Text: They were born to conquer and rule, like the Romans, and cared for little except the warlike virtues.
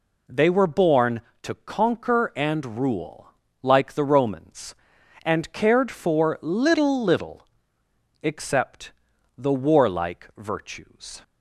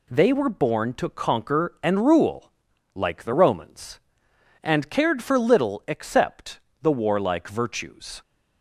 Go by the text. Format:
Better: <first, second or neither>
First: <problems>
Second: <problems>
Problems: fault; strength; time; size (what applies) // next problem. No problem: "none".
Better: second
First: says "little" twice; at 7.0 s // pauses between "except" and "the"; noticeable; at 8.9 s; 0.46 s long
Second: pauses between "except" and "the"; slight; at 6.5 s; 0.22 s long